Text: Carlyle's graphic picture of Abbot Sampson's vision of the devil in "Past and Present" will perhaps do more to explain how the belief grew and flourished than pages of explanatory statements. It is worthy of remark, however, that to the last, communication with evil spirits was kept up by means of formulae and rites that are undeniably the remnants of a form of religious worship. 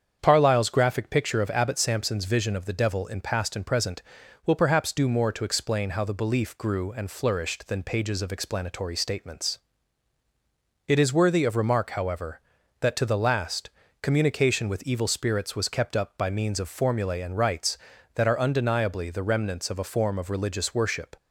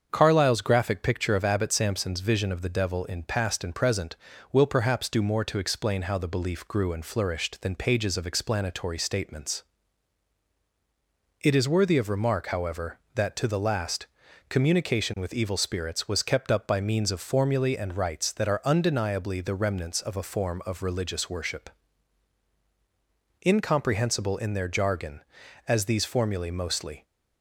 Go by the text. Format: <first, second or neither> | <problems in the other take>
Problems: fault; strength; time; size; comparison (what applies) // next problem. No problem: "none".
first | starts louder than the rest; strong; until 1.1 s; 7 dB; strong in the first // goes on to say "Incomprehensible in their jargon as these formulae mostly"; strong; from 23.4 s on; 3.6 s long